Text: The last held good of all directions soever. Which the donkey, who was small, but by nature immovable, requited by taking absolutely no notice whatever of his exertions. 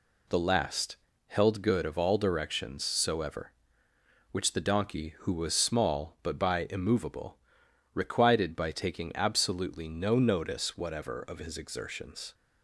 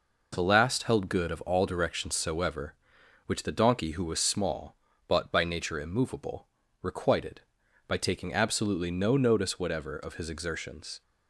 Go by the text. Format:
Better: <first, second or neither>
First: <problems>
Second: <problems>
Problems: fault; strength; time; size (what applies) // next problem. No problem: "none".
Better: second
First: pauses between "last" and "held"; slight; at 0.9 s; 0.30 s long // skips "nature"; at 6.6 s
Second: none